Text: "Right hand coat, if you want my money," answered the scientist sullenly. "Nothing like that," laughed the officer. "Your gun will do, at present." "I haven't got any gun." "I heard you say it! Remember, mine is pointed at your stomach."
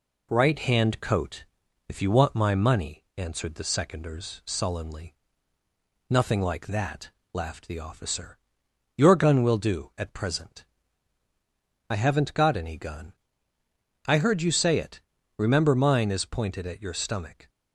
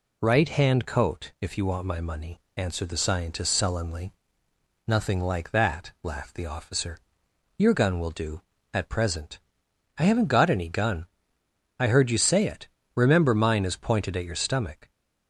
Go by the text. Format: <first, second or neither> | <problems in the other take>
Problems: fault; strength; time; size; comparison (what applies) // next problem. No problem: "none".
second | says "seconders" for "scientist"; at 3.6 s